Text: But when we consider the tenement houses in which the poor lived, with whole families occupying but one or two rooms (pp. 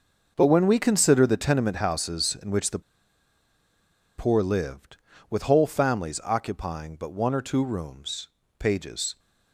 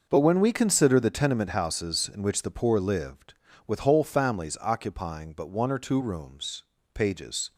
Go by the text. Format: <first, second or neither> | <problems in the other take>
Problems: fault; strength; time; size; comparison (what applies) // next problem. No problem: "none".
second | pauses between "the" and "poor"; strong; at 2.7 s; 1.3 s long